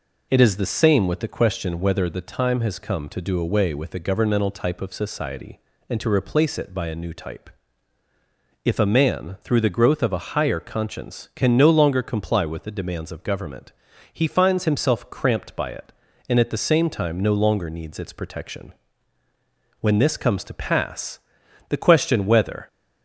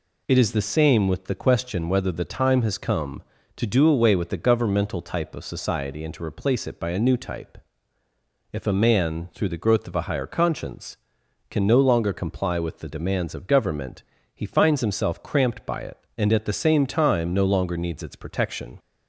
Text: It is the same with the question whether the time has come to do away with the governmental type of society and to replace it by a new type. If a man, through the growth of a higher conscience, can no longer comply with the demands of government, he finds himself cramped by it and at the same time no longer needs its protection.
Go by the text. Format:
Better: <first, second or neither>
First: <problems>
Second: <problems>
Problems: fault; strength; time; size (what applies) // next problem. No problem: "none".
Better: second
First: goes on to say "When this comes to pass the question whether"; strong; from 19.7 s on; 2.8 s long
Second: none